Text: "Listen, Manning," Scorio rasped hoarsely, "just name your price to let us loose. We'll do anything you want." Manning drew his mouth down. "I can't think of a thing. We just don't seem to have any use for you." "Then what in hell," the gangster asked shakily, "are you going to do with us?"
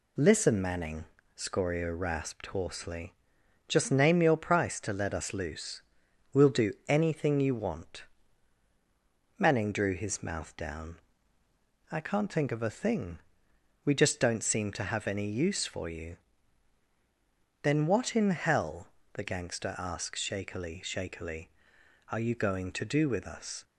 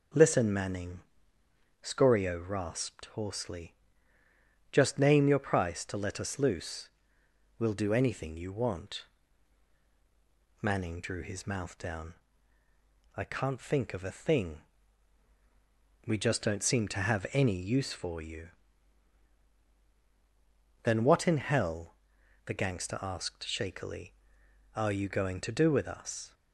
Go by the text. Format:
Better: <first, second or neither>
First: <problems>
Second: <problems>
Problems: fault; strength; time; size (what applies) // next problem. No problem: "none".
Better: second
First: says "shakily" twice; at 20.8 s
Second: none